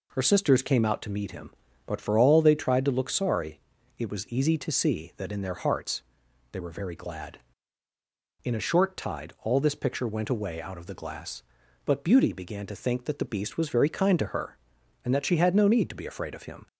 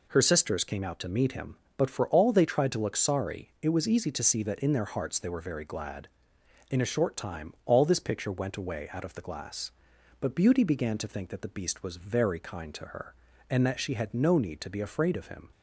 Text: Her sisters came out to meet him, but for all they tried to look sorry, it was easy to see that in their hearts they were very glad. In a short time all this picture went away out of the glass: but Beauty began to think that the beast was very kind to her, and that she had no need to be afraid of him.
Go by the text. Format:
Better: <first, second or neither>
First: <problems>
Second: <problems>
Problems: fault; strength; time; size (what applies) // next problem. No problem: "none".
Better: second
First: pauses between "hearts" and "they"; noticeable; at 6.0 s; 0.50 s long // says "tide" for "time"; at 8.9 s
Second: none